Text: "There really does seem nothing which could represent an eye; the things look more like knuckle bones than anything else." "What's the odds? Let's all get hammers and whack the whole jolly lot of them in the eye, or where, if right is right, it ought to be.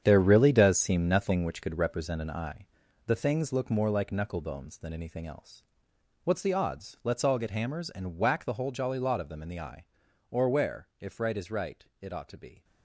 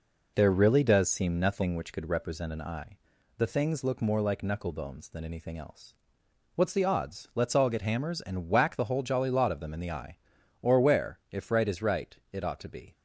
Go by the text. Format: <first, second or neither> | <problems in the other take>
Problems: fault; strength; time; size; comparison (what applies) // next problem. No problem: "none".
second | gets quieter; strong; throughout; 11.5 dB